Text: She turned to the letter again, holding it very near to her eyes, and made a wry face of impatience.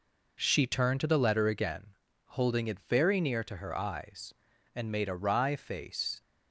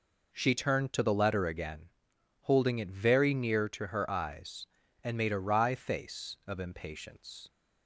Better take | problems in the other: second | stops before "of impatience"; at 6.2 s

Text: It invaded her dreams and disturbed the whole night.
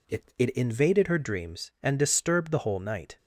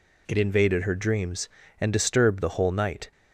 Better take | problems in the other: second | says "It" twice; at 0.3 s

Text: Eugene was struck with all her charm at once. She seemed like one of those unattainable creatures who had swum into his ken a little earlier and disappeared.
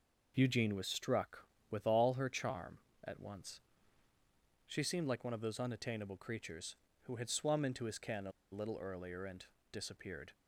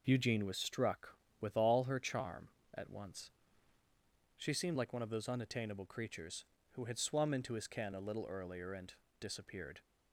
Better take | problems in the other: second | pauses between "a" and "little"; slight; at 8.3 s; 0.21 s long // pauses between "and" and "disappeared"; slight; at 9.4 s; 0.28 s long; slight in the second

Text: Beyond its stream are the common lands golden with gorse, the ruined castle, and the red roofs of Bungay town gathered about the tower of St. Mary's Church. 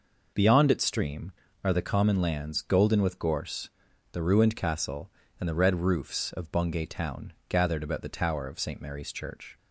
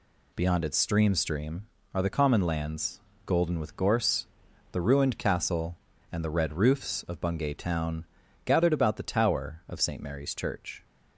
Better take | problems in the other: first | says "stream" twice; at 1.1 s // pauses between "lands" and "golden"; slight; at 3.0 s; 0.26 s long // pauses between "town" and "gathered"; at 8.0 s; 0.40 s long; slight in the first

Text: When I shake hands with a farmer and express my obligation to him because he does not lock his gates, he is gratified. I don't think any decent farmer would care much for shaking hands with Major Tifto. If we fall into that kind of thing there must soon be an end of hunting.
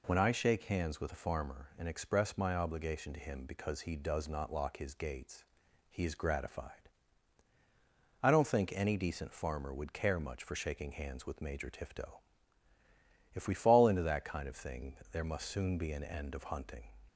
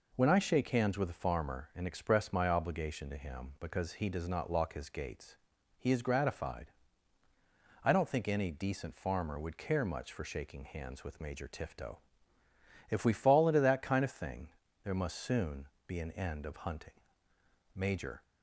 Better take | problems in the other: first | pauses between "thing" and "there"; slight; at 14.4 s; 0.34 s long // pauses between "soon" and "be"; slight; at 15.6 s; 0.22 s long // goes on to say "Major"; slight; from 17.7 s on; 0.48 s long

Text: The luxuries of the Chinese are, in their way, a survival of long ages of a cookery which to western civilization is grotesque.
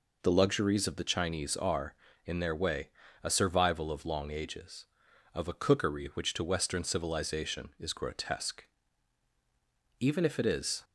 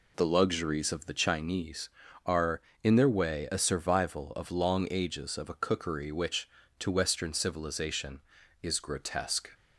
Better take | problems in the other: second | goes on to say "Even if it is"; noticeable; from 9.9 s on; 0.84 s long

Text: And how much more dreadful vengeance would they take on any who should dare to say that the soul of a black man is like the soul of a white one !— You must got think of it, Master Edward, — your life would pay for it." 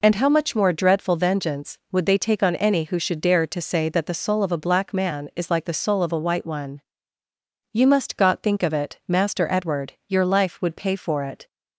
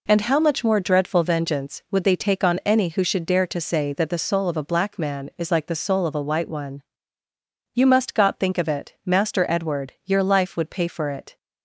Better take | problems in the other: neither | none

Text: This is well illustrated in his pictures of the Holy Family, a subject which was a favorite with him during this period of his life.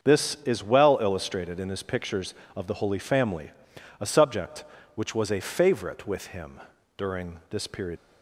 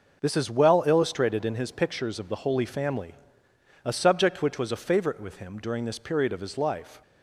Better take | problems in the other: second | starts louder than the rest; until 1.1 s; 7 dB // pauses between "him" and "during"; at 6.5 s; 0.38 s long // stops before "of his life"; at 7.9 s

